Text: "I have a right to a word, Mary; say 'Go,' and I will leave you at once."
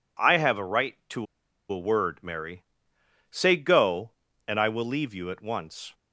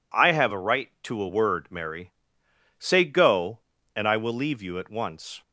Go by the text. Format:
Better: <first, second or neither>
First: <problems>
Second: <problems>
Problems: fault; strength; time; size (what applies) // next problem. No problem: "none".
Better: second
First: pauses between "to" and "a"; noticeable; at 1.2 s; 0.46 s long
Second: none